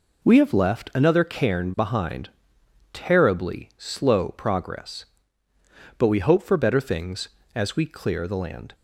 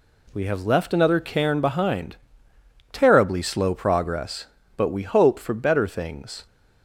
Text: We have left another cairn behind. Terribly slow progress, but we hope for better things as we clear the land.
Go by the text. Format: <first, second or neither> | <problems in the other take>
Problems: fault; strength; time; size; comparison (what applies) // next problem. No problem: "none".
first | stops before "as we clear the land"; at 6.4 s